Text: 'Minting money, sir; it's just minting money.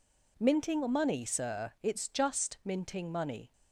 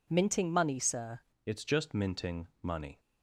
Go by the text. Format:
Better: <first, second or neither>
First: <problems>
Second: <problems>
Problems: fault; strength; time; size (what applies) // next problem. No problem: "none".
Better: first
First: none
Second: changes voice at "it's"; from 1.4 s on; 1.5 s long // pauses between "minting" and "money"; slight; at 2.4 s; 0.16 s long